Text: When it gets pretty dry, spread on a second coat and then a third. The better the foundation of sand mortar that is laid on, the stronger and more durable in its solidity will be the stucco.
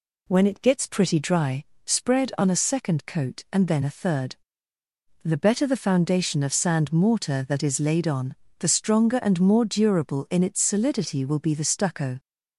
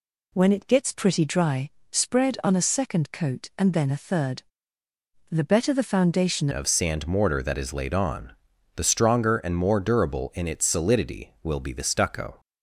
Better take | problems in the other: first | changes voice at "of"; from 6.5 s on; 5.8 s long

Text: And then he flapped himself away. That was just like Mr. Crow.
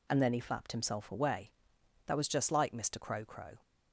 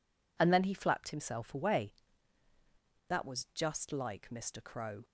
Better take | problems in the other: second | says "Crow" twice; at 3.2 s

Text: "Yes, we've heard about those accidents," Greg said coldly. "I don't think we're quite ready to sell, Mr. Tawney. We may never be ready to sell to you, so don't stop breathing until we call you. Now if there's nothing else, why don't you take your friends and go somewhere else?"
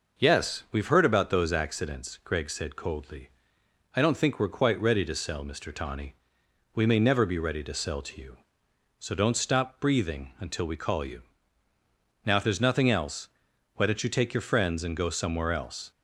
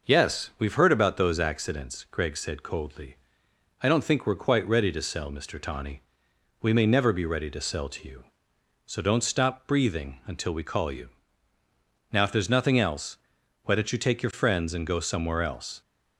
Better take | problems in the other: neither | none

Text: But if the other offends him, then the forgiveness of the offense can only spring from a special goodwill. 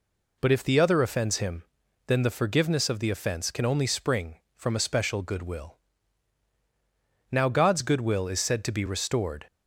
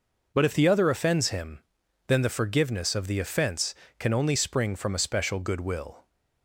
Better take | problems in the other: second | goes on to say "Now God's goodwill is said to be restored"; strong; from 7.3 s on; 2.1 s long

